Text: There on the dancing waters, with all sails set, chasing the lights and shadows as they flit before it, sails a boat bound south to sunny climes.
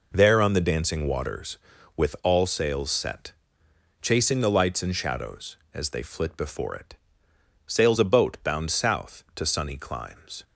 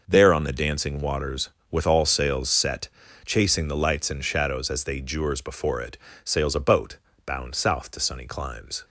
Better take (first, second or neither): first